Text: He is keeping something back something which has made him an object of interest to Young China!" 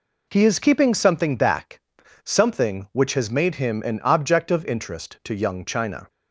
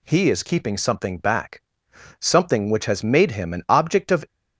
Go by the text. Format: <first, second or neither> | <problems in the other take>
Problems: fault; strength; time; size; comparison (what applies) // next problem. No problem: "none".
first | pauses between "back" and "something"; noticeable; at 1.6 s; 0.56 s long; also in the first // stops before "interest to Young China"; at 4.2 s